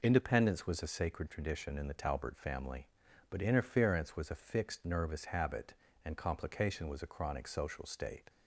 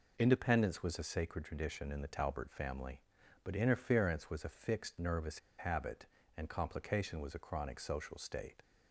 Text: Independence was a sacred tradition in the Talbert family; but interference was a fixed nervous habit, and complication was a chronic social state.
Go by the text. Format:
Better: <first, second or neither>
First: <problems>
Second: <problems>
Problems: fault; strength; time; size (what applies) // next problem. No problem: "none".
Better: first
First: none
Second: pauses between "nervous" and "habit"; slight; at 5.3 s; 0.19 s long